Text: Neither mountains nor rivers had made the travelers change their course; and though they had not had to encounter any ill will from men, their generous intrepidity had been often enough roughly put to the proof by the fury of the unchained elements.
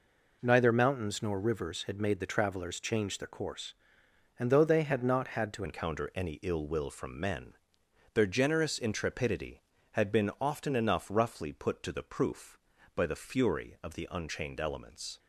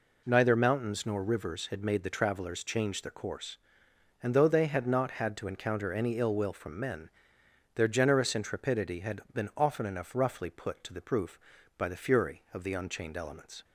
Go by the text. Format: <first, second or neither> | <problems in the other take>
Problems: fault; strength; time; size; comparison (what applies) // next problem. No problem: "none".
second | changes voice at "encounter"; from 5.6 s on; 9.5 s long